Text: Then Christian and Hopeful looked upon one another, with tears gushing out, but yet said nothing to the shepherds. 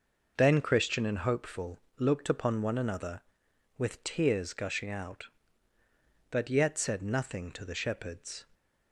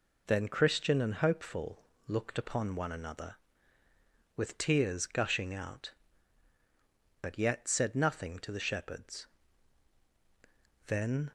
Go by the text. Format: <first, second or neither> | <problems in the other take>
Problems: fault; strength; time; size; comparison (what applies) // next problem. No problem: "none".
first | pauses between "Hopeful" and "looked"; slight; at 1.8 s; 0.22 s long; slight in the first // goes on to say "Then"; slight; from 10.8 s on; 0.44 s long